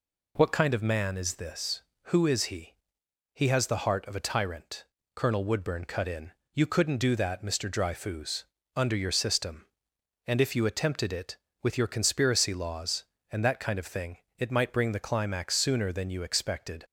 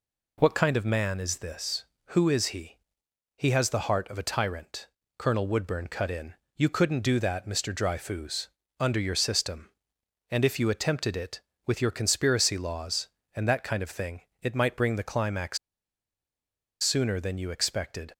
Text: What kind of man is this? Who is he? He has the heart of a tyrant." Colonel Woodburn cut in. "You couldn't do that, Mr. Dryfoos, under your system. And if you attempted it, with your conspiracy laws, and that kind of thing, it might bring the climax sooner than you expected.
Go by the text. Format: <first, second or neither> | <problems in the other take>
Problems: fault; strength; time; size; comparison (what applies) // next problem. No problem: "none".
first | pauses between "climax" and "sooner"; at 15.5 s; 1.2 s long